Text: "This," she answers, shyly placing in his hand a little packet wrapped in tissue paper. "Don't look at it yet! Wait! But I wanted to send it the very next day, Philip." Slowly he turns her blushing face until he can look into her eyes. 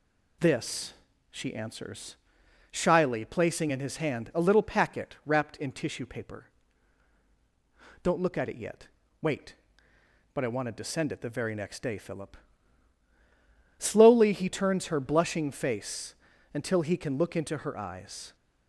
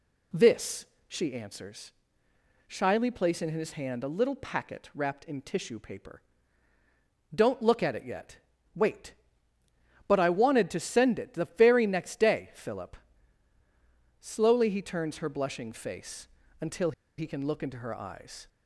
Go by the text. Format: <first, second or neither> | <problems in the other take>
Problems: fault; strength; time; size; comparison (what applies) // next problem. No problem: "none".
first | pauses between "face" and "until"; slight; at 16.2 s; 0.32 s long; also in the first // pauses between "until" and "he"; slight; at 16.9 s; 0.25 s long